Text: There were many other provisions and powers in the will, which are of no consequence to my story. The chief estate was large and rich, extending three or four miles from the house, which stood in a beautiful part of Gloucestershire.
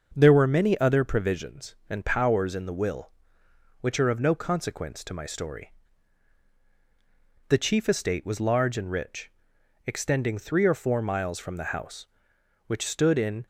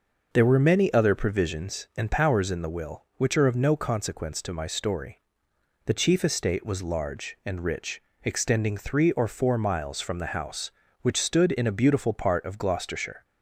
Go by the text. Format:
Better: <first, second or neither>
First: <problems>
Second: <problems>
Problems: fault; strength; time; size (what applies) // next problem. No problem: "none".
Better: second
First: starts louder than the rest; noticeable; until 1.1 s; 6 dB // stops before "a beautiful part of Gloucestershire"; at 13.4 s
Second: none